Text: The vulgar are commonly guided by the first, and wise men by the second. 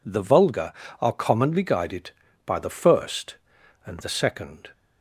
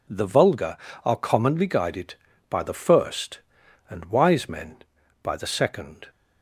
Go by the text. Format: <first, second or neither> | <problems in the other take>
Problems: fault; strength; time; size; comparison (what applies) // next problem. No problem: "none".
second | skips "wise men by"; at 4.0 s